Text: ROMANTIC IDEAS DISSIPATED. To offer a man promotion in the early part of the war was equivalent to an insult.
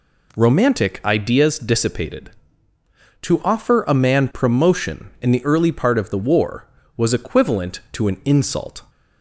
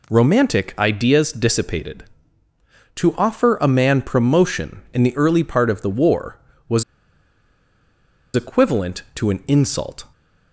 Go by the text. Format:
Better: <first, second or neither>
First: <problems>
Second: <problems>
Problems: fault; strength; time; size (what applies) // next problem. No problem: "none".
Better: first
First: none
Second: pauses between "was" and "equivalent"; strong; at 6.8 s; 1.5 s long